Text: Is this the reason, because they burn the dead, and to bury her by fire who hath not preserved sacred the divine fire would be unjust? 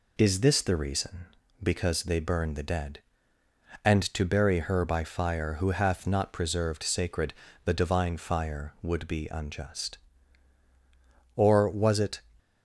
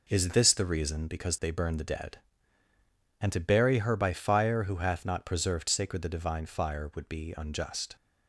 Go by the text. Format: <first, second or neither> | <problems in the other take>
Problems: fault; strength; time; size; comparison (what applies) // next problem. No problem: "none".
second | pauses between "sacred" and "the"; slight; at 7.3 s; 0.32 s long // goes on to say "Or was it"; noticeable; from 11.3 s on; 0.86 s long